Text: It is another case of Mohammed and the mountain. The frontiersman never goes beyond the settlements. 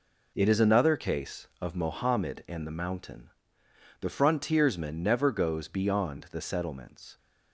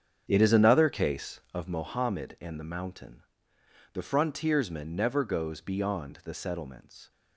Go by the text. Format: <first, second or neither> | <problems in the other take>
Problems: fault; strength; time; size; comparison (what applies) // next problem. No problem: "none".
first | starts louder than the rest; strong; until 1.7 s; 7.5 dB